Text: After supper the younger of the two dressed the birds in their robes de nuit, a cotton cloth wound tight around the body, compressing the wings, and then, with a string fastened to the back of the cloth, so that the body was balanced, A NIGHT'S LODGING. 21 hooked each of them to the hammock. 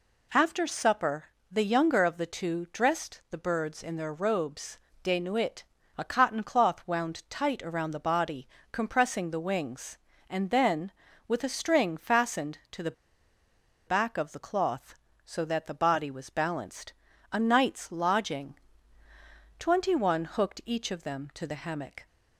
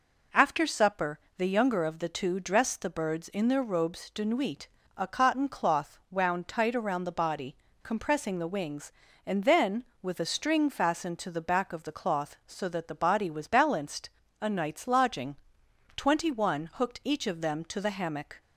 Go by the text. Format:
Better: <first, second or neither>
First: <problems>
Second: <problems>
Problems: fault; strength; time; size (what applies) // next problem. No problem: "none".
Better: second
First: pauses between "supper" and "the"; slight; at 1.2 s; 0.24 s long // pauses between "robes" and "de"; slight; at 4.7 s; 0.24 s long // pauses between "the" and "back"; noticeable; at 12.9 s; 0.95 s long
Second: pauses between "supper" and "the"; slight; at 1.1 s; 0.20 s long